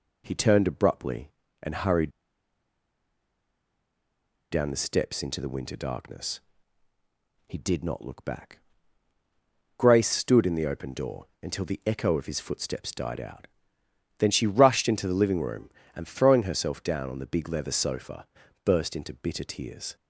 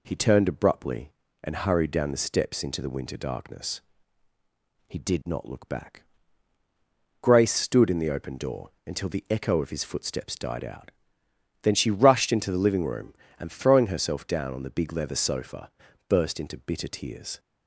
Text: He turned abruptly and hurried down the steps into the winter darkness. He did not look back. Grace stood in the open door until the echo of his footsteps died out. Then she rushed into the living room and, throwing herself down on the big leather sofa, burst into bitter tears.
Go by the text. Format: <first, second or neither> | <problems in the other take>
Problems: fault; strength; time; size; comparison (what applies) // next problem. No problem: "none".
second | pauses between "hurried" and "down"; strong; at 2.0 s; 2.4 s long // pauses between "door" and "until"; slight; at 11.2 s; 0.16 s long; slight in the second